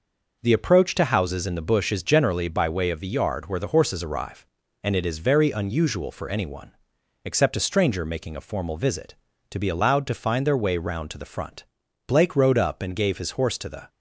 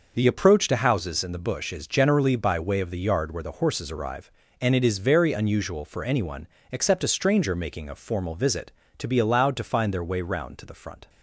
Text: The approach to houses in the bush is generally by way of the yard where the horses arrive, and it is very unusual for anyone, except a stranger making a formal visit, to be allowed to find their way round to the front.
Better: second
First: goes on to say "Blake rode up and gave his horse to the"; strong; from 12.0 s on; 1.8 s long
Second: none

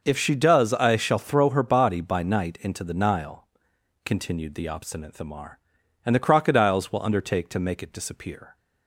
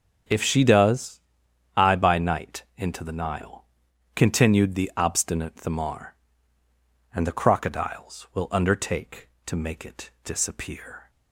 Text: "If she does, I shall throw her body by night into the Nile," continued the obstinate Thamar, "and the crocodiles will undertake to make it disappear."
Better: first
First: none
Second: starts louder than the rest; strong; until 1.8 s; 7.5 dB // skips "shall throw her body"; at 1.9 s

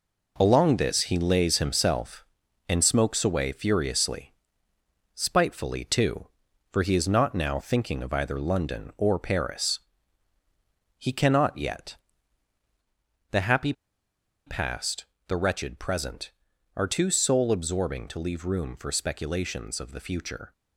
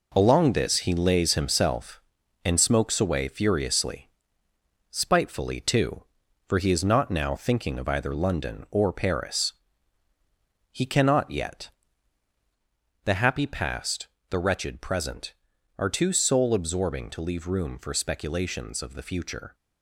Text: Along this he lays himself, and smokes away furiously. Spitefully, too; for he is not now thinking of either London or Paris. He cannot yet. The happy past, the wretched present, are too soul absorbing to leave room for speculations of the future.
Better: second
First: pauses between "happy" and "past"; noticeable; at 13.7 s; 0.73 s long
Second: none

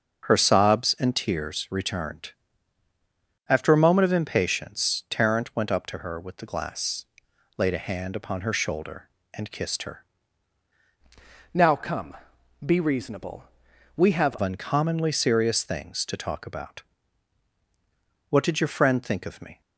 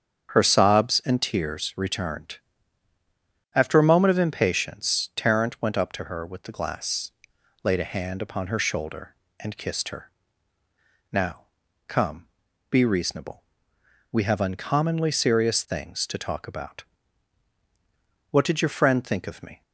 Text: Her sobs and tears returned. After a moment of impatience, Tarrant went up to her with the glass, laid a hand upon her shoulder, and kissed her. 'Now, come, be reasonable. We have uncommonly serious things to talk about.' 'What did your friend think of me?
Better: second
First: starts louder than the rest; until 1.2 s; 6 dB // changes voice from "Now" to "have"; from 11.5 to 14.3 s; 2.8 s long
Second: starts louder than the rest; strong; until 1.3 s; 7.5 dB

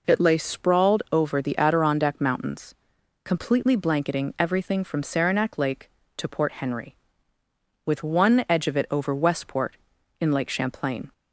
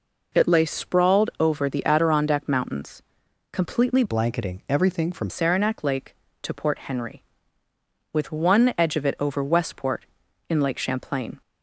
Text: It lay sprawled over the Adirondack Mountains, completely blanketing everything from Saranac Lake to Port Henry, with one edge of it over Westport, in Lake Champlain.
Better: first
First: none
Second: changes voice from "blanketing" to "from"; from 4.0 to 5.2 s; 1.2 s long

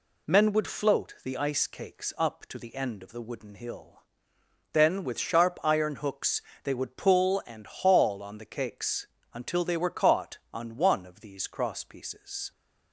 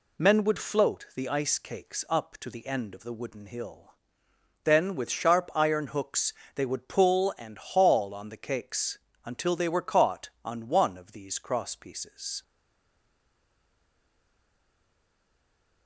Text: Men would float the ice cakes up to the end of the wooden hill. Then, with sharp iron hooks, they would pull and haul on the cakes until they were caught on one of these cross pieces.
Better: first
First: pauses between "cakes" and "until"; slight; at 9.0 s; 0.26 s long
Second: pauses between "cakes" and "until"; slight; at 8.9 s; 0.26 s long // stays silent after the last word; strong; from 12.4 s on; 3.4 s long

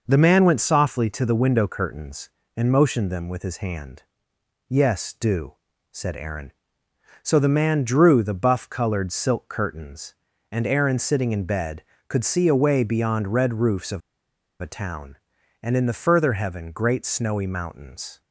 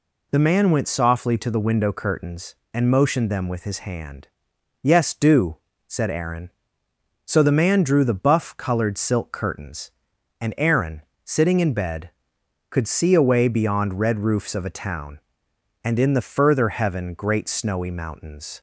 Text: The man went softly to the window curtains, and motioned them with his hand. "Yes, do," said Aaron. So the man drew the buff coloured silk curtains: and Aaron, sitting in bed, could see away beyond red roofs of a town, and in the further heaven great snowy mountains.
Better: second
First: pauses between "of" and "a"; noticeable; at 14.0 s; 0.62 s long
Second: none

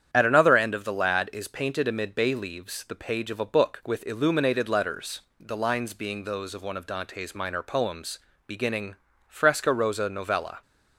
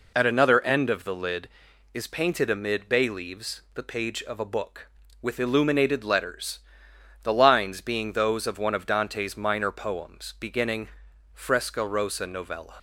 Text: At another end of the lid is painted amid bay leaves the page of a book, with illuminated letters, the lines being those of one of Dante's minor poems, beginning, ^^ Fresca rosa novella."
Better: second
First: starts louder than the rest; strong; until 1.1 s; 9 dB // says "lad" for "lid"; at 0.9 s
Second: none

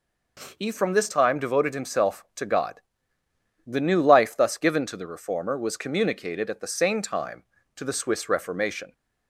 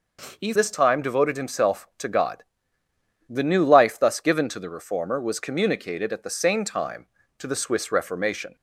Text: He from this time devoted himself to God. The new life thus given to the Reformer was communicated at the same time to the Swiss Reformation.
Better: first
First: none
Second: skips "from"; at 0.5 s

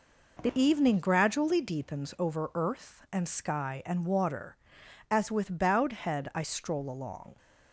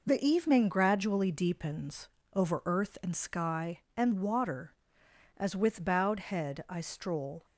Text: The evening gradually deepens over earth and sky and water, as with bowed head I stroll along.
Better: first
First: none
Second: pauses between "deepens" and "over"; slight; at 2.0 s; 0.24 s long // stops before "along"; at 7.4 s

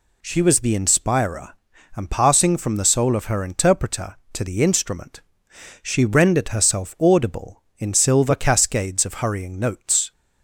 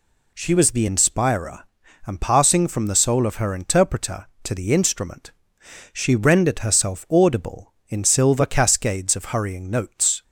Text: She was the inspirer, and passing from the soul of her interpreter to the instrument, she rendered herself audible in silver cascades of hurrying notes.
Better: neither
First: none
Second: none

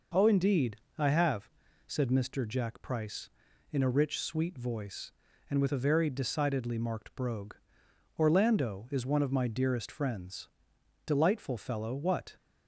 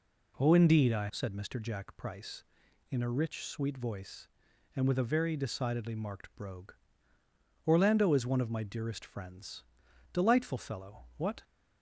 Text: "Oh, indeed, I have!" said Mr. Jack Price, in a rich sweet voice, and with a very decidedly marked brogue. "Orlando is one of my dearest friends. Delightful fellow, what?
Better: first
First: none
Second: skips "have"; at 1.0 s

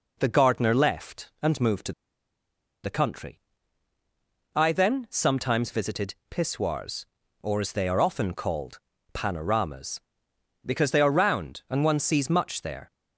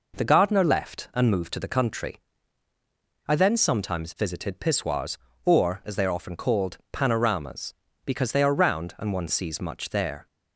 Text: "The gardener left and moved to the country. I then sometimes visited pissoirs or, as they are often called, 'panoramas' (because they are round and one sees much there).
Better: second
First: pauses between "to" and "the"; noticeable; at 1.9 s; 0.92 s long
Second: none

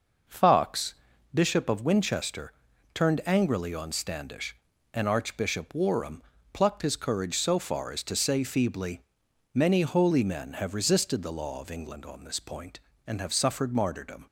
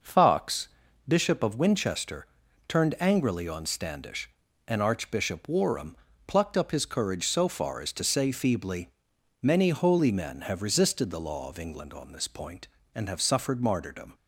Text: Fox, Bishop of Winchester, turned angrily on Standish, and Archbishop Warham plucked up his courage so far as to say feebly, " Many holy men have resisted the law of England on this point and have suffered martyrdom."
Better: second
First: pauses between "Warham" and "plucked"; slight; at 6.2 s; 0.30 s long // skips "up"; at 6.8 s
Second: pauses between "Warham" and "plucked"; slight; at 5.9 s; 0.30 s long

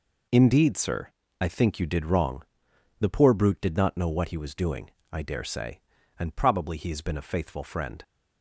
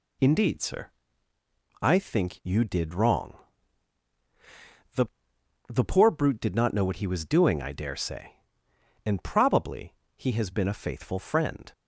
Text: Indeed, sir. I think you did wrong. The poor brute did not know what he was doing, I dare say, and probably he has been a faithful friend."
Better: first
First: none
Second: says "The" twice; at 5.6 s // pauses between "probably" and "he"; slight; at 9.9 s; 0.22 s long

